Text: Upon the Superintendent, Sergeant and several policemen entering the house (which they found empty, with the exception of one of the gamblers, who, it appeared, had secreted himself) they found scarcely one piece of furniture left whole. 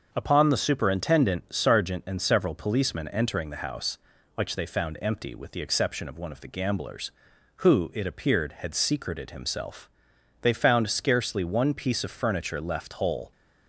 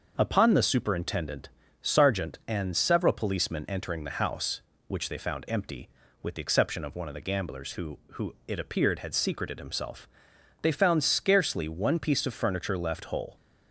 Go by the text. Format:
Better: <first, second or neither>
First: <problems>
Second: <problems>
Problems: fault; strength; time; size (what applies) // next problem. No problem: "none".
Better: first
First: starts louder than the rest; until 1.1 s; 6.5 dB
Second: starts louder than the rest; until 1.1 s; 6.5 dB // says "who" twice; at 8.1 s